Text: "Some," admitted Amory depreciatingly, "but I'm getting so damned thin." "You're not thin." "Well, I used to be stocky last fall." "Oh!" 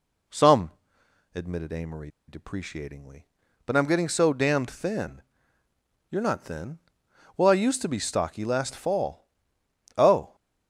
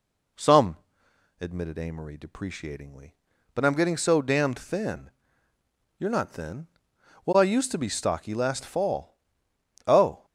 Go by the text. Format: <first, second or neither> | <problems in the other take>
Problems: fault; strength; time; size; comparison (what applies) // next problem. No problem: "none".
second | pauses between "Amory" and "depreciatingly"; slight; at 2.0 s; 0.18 s long